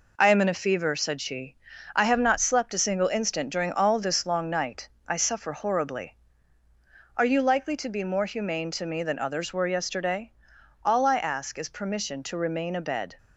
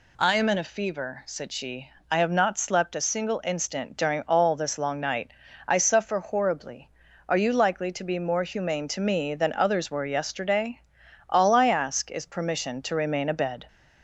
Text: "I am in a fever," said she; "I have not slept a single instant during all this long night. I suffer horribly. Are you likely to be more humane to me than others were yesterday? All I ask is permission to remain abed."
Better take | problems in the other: second | gets quieter; noticeable; throughout; 5 dB

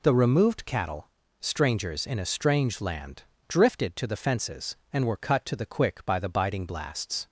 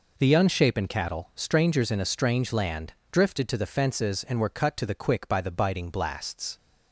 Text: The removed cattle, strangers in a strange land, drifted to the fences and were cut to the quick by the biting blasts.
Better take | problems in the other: first | says "unshapen" for "removed"; at 0.3 s

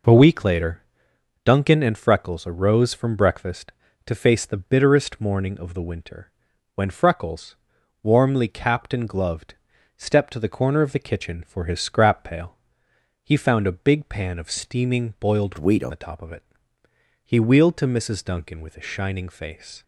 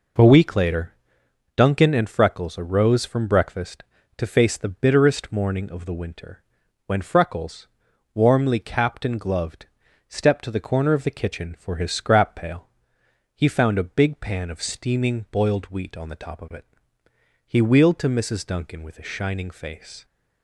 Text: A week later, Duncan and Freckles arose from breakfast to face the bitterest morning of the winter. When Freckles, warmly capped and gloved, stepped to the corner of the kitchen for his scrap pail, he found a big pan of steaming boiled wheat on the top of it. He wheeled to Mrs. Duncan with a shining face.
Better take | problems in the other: second | changes voice from "wheat" to "on"; from 15.5 to 15.9 s; 0.4 s long

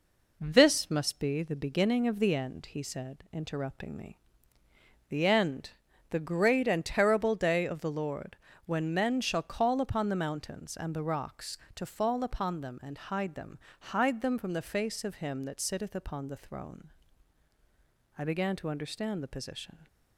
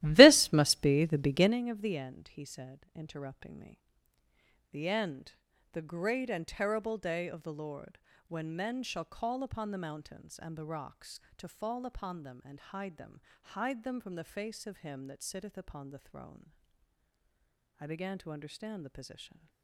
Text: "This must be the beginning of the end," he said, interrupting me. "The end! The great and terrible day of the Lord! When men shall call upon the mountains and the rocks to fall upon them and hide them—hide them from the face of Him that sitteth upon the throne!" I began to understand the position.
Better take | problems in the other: first | starts louder than the rest; strong; until 1.6 s; 16 dB

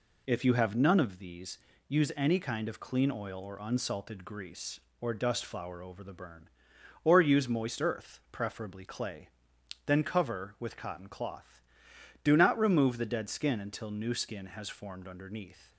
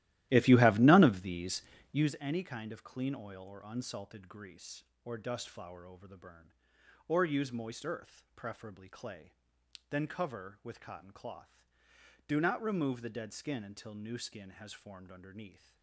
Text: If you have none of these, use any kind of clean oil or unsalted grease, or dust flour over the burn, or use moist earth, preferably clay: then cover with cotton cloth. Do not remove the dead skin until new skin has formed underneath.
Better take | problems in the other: first | starts louder than the rest; strong; until 2.2 s; 15 dB

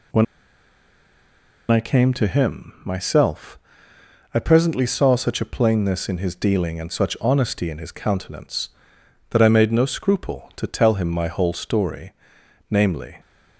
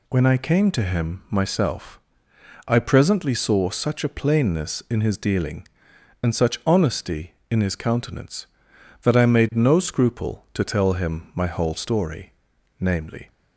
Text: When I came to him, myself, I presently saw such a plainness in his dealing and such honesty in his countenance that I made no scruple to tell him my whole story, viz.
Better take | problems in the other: second | pauses between "When" and "I"; strong; at 0.2 s; 1.4 s long

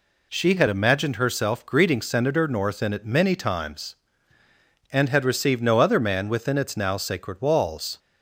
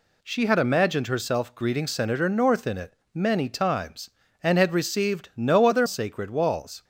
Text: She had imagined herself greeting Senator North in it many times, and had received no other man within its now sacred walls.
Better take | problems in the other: first | pauses between "it" and "many"; slight; at 2.9 s; 0.20 s long // skips "man within its now"; at 5.8 s

